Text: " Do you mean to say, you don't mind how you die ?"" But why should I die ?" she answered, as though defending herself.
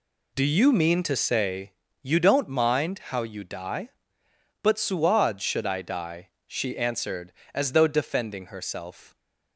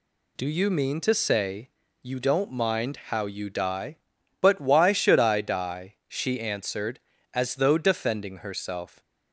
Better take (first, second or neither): second